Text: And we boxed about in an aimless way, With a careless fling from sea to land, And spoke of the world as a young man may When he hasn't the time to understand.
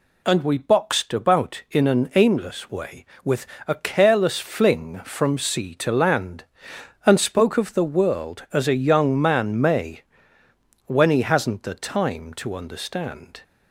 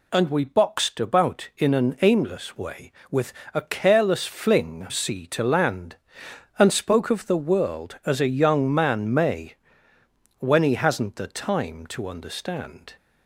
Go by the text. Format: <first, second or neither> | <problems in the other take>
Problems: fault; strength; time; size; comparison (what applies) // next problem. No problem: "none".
first | pauses between "With" and "a"; slight; at 3.3 s; 0.22 s long; slight in the first // skips "from"; at 4.8 s // pauses between "may" and "When"; noticeable; at 9.5 s; 0.84 s long; noticeable in the first